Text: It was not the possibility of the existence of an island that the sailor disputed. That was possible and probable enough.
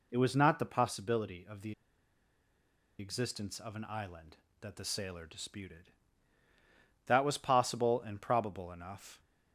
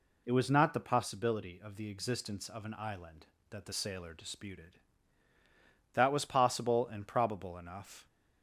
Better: second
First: pauses between "the" and "existence"; strong; at 1.7 s; 1.2 s long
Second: none

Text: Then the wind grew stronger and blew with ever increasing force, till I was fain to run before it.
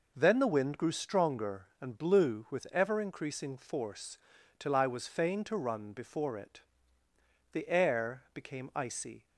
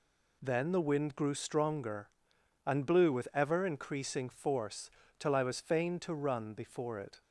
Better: second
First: goes on to say "The air became icy"; strong; from 7.5 s on; 1.7 s long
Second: none

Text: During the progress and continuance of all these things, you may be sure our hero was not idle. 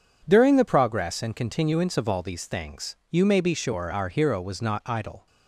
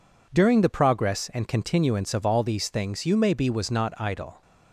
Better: first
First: none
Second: skips "sure our hero"; at 3.4 s

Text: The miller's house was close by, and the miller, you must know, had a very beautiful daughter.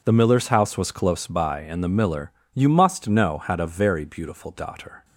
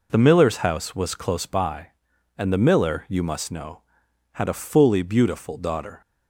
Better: first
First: none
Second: says "fully" for "very"; at 4.6 s

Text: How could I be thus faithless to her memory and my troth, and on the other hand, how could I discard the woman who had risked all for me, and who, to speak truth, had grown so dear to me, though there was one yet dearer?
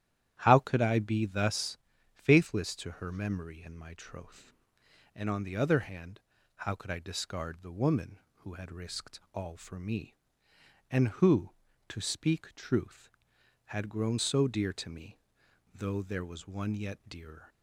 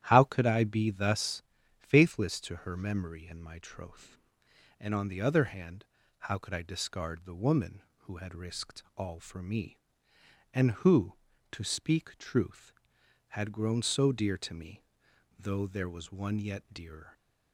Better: neither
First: starts louder than the rest; strong; until 1.4 s; 11.5 dB // pauses between "thus" and "faithless"; slight; at 1.7 s; 0.36 s long // pauses between "risked" and "all"; slight; at 9.1 s; 0.16 s long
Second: starts louder than the rest; strong; until 1.0 s; 11 dB // pauses between "thus" and "faithless"; slight; at 1.4 s; 0.36 s long // pauses between "risked" and "all"; slight; at 8.8 s; 0.16 s long

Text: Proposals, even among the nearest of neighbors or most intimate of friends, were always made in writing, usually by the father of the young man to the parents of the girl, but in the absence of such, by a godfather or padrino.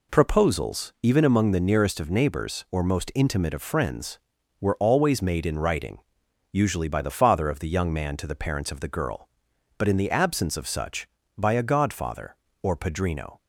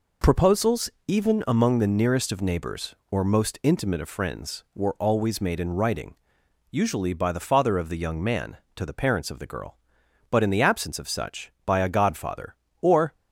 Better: first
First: none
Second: stops before "padrino"; at 13.1 s

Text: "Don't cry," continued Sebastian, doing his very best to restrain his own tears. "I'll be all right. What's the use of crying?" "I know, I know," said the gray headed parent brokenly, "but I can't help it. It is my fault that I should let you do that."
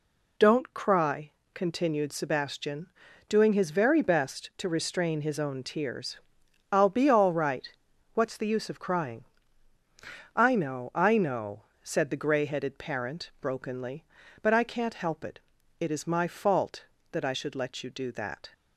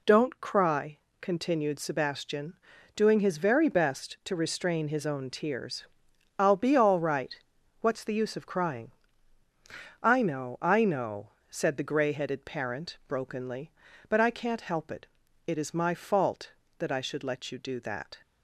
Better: neither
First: none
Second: none

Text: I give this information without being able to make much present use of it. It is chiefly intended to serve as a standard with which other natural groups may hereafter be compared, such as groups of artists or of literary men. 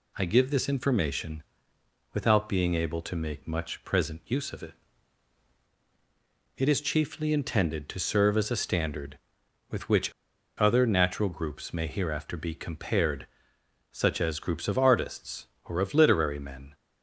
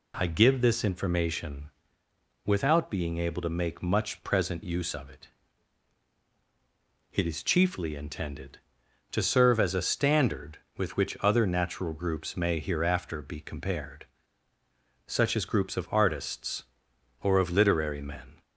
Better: second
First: pauses between "information" and "without"; noticeable; at 1.4 s; 0.72 s long // pauses between "which" and "other"; noticeable; at 10.1 s; 0.47 s long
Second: pauses between "information" and "without"; noticeable; at 1.6 s; 0.76 s long

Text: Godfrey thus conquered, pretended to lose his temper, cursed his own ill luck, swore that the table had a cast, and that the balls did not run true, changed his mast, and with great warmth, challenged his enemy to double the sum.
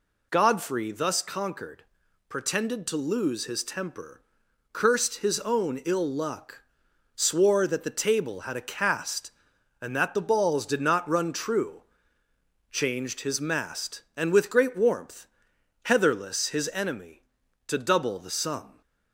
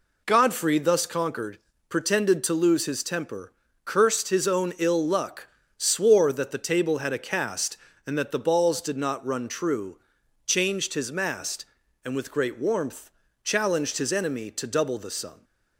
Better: second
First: says "heatherless" for "challenged"; at 15.8 s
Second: none

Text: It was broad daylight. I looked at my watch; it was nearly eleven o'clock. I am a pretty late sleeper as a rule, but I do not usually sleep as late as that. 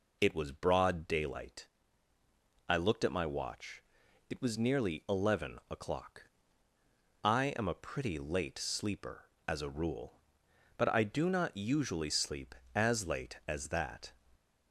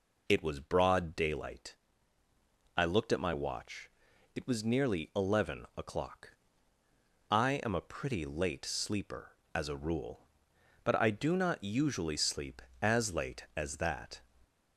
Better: neither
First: none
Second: none

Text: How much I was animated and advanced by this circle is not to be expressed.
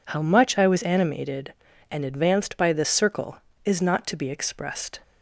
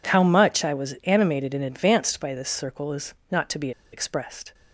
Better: first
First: none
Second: pauses between "is" and "not"; slight; at 3.1 s; 0.16 s long // pauses between "be" and "expressed"; slight; at 3.7 s; 0.22 s long

